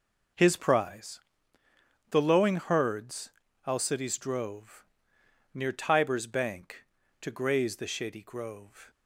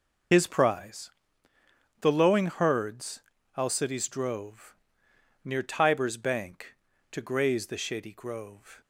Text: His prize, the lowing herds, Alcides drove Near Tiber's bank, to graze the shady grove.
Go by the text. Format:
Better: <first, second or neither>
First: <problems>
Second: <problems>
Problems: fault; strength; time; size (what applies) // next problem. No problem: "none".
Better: first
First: pauses between "drove" and "Near"; noticeable; at 4.8 s; 0.70 s long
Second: loses the start of "His"; at 0.3 s; 50 ms // pauses between "drove" and "Near"; noticeable; at 4.7 s; 0.70 s long